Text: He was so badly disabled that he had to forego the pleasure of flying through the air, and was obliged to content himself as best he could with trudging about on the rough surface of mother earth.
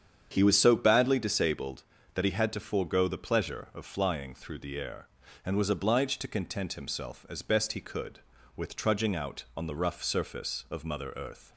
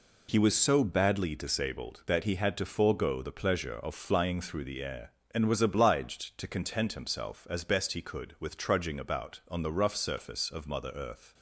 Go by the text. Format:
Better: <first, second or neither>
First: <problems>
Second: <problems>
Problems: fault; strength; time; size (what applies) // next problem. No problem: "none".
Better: second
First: starts louder than the rest; strong; until 1.3 s; 8 dB // says "out" for "about"; at 9.1 s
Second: none